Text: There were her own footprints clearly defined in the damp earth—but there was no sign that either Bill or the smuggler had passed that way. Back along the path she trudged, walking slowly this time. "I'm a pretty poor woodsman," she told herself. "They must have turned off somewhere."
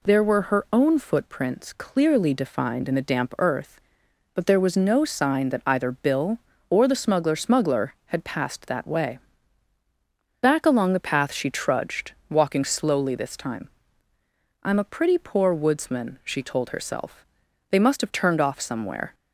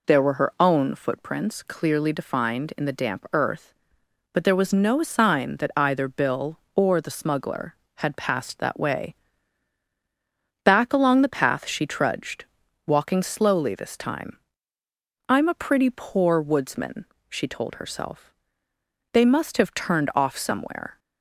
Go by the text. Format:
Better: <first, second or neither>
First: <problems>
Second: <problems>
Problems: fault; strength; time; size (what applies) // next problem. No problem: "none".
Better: second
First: says "smuggler" twice; at 7.3 s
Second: none